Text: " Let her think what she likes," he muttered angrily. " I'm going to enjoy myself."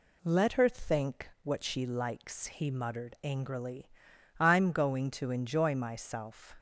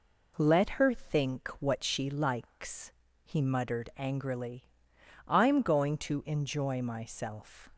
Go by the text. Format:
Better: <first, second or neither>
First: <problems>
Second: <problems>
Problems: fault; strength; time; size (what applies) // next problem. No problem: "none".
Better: neither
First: none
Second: none